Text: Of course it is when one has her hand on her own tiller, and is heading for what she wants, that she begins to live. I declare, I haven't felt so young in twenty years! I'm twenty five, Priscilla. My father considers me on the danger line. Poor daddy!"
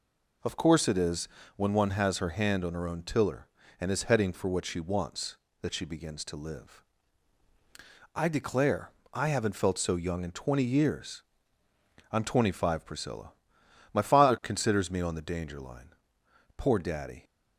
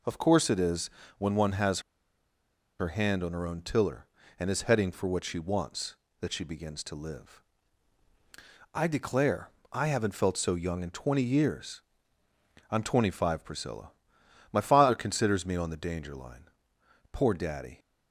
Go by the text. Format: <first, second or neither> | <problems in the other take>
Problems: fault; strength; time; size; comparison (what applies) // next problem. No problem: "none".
first | pauses between "is" and "when"; slight; at 0.8 s; 0.28 s long; slight in the first // pauses between "has" and "her"; at 1.7 s; 0.99 s long